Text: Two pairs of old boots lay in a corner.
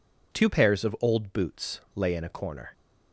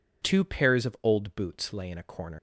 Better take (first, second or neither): first